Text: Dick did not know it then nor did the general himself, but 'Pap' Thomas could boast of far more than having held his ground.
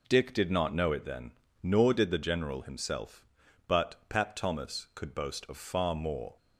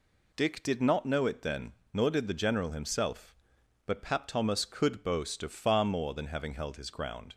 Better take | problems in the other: second | pauses between "then" and "nor"; slight; at 1.3 s; 0.30 s long; slight in the second // stops before "than having held his ground"; at 6.3 s

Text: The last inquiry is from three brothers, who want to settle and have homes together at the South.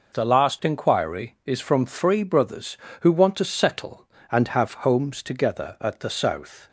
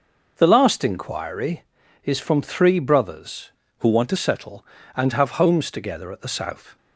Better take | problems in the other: first | changes voice from "who" to "to"; from 3.8 to 4.1 s; 0.3 s long

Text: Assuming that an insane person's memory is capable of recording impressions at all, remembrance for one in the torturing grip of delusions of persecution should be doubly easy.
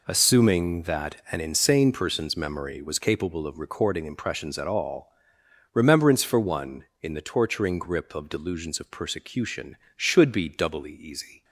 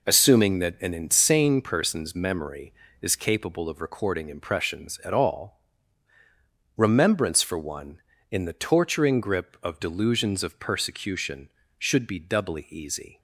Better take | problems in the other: second | pauses between "that" and "an"; slight; at 1.1 s; 0.16 s long // says "was" for "is"; at 2.8 s

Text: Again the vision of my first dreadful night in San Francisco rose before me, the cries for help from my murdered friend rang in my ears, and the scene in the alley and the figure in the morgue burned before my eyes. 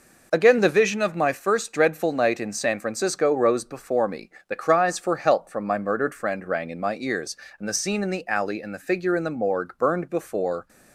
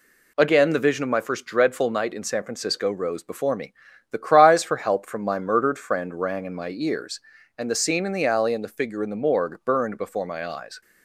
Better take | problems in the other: second | stops before "my eyes"; at 10.6 s

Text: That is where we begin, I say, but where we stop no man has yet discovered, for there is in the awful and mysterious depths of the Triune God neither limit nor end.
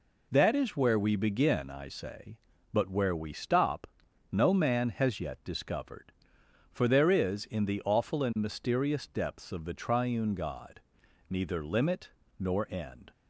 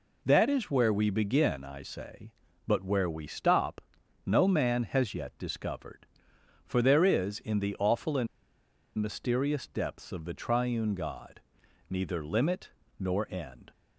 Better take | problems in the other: first | pauses between "stop" and "no"; noticeable; at 3.8 s; 0.46 s long; noticeable in the first // pauses between "and" and "mysterious"; noticeable; at 8.2 s; 0.71 s long // pauses between "God" and "neither"; noticeable; at 11.3 s; 0.48 s long; noticeable in the first // pauses between "limit" and "nor"; slight; at 12.7 s; 0.28 s long; slight in the first

